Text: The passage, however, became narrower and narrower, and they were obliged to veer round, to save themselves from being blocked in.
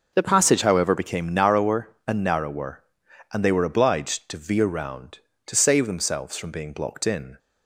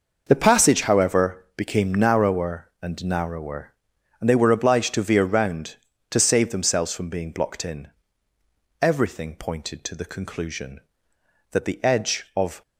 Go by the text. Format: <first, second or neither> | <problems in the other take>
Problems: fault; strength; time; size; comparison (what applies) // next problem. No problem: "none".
first | goes on to say "Everything pointed to the conclusion that the edge of"; strong; from 8.8 s on; 3.8 s long